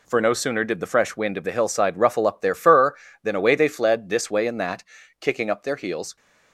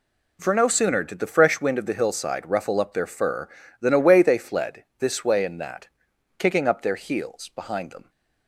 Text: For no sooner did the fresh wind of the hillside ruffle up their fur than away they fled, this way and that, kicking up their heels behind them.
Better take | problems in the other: second | stops before "behind them"; at 6.1 s

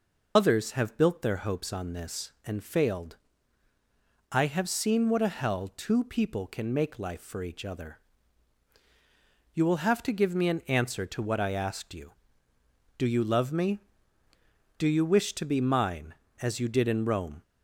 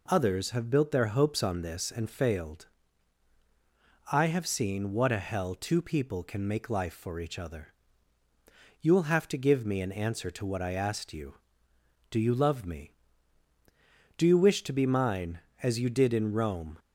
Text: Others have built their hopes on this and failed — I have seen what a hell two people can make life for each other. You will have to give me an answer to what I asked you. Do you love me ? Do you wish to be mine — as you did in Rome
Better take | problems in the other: second | loses the start of "Others"; at 0.3 s; 30 ms

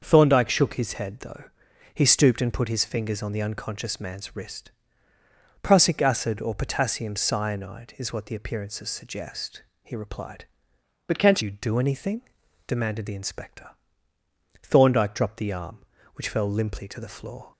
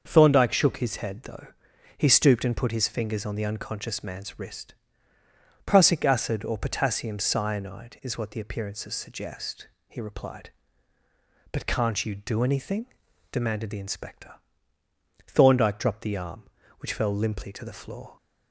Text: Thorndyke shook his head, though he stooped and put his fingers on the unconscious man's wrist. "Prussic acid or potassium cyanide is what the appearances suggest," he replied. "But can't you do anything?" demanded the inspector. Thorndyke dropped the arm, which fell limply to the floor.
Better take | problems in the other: second | starts louder than the rest; until 1.0 s; 6.5 dB; also in the second // pauses between "though" and "he"; noticeable; at 1.4 s; 0.50 s long; noticeable in the second // changes voice from "But" to "can't"; from 11.0 to 11.4 s; 0.4 s long

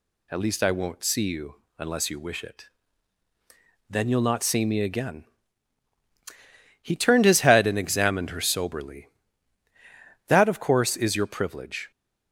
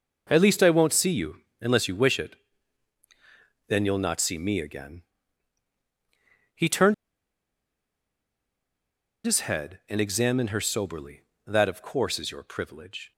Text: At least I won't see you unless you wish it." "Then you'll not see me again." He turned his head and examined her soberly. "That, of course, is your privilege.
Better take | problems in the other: first | pauses between "you" and "unless"; slight; at 1.3 s; 0.22 s long; slight in the first // pauses between "turned" and "his"; strong; at 6.9 s; 2.3 s long

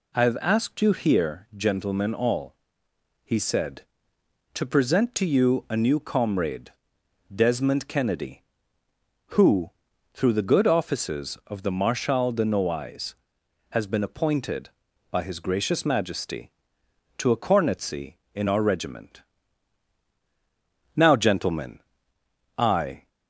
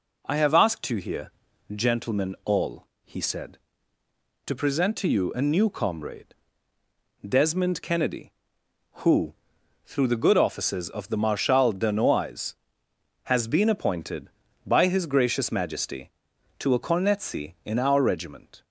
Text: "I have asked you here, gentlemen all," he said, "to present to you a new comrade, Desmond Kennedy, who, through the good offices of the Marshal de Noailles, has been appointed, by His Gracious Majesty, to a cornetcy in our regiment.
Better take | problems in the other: second | goes on to say "Now gentlemen I"; strong; from 20.9 s on; 2.1 s long

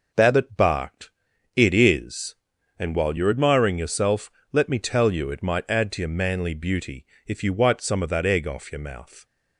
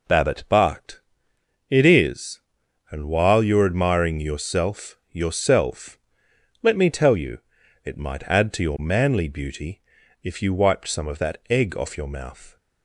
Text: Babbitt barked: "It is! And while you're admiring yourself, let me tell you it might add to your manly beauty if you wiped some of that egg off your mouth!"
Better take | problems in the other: first | says "yourself" twice; at 5.1 s // pauses between "you" and "it"; noticeable; at 7.3 s; 0.46 s long // pauses between "beauty" and "if"; at 9.8 s; 0.42 s long; slight in the first

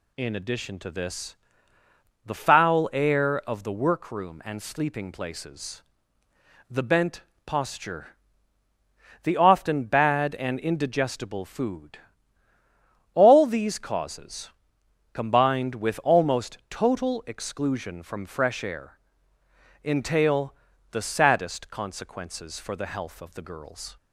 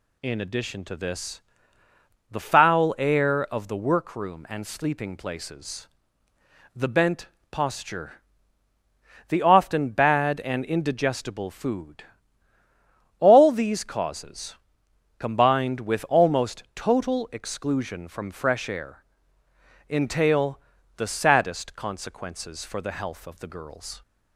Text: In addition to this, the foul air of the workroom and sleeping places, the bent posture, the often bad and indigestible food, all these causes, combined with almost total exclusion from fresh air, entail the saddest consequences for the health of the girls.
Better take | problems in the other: neither | pauses between "bent" and "posture"; slight; the same in both // pauses between "entail" and "the"; slight; the same in both

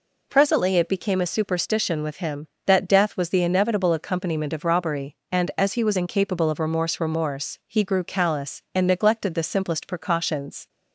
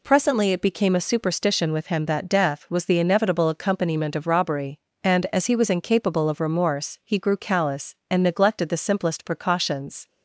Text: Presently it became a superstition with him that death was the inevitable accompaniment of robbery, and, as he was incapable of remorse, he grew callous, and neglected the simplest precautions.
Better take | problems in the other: second | says "remorse" twice; at 7.0 s

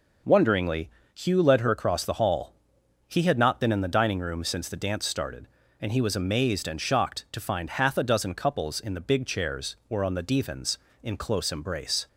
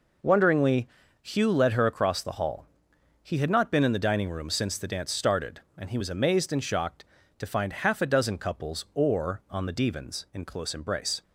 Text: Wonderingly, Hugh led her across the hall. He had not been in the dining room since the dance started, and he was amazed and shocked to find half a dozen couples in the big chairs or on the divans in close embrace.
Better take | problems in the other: first | skips "in the big chairs"; at 8.8 s

